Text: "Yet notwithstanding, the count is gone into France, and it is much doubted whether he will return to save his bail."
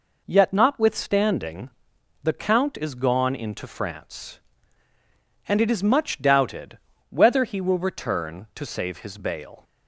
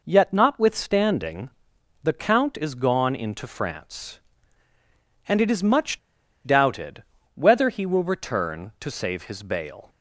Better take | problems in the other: first | pauses between "much" and "doubted"; noticeable; at 5.9 s; 0.47 s long // pauses between "doubted" and "whether"; slight; at 7.0 s; 0.30 s long; slight in the first

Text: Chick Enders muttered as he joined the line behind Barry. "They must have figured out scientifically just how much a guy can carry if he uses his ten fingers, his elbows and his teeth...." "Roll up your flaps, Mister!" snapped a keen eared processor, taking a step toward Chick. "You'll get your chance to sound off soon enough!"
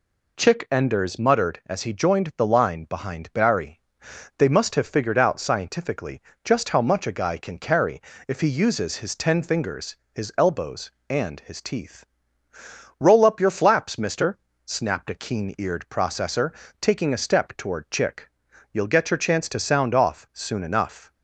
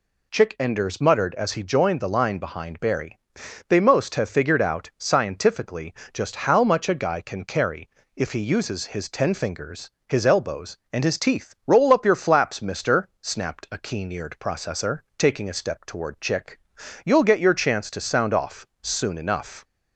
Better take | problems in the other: first | says "most" for "must"; at 3.7 s // pauses between "scientifically" and "just"; slight; at 5.9 s; 0.20 s long; slight in the first // pauses between "carry" and "if"; slight; at 7.8 s; 0.28 s long; slight in the first // pauses between "off" and "soon"; slight; at 18.6 s; 0.16 s long

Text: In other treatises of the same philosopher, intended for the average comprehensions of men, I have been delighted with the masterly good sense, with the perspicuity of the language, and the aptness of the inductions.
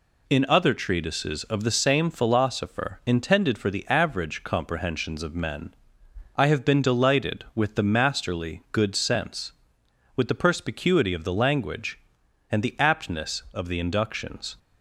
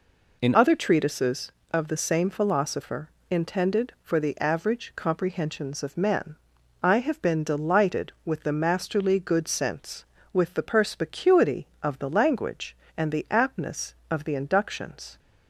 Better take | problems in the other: first | changes voice at "other"; from 0.5 s on; 14.6 s long

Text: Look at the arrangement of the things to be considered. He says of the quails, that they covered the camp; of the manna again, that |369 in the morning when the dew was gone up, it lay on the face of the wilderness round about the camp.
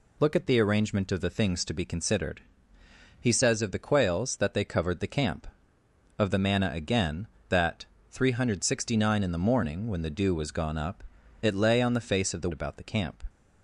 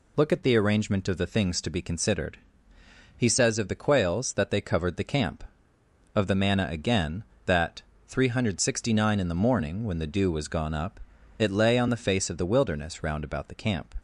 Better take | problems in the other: second | skips "wilderness round"; at 12.5 s

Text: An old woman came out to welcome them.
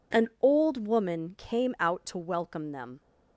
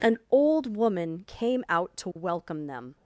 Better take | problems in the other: neither | none

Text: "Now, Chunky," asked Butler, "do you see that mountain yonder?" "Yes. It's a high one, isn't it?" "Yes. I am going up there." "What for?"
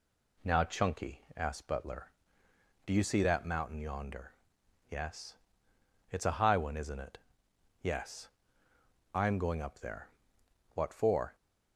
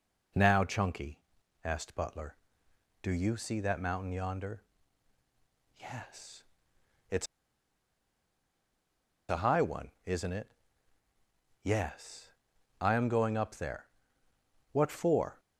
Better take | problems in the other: first | pauses between "It's" and "a"; strong; at 7.2 s; 2.0 s long

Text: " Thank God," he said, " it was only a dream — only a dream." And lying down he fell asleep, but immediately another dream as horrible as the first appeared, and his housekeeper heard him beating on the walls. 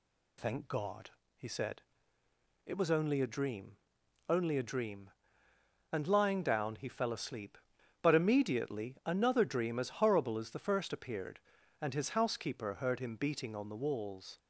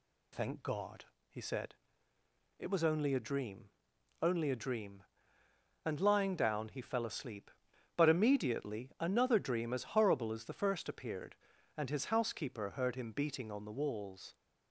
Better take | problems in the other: neither | none

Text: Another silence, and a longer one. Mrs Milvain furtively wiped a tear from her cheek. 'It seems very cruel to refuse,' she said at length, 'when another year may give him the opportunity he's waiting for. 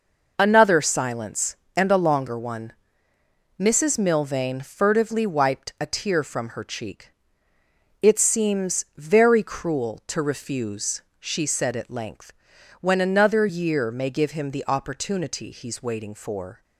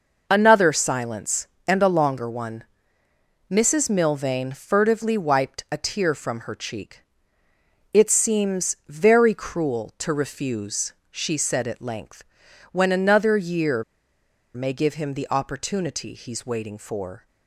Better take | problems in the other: first | pauses between "year" and "may"; noticeable; at 13.8 s; 0.71 s long

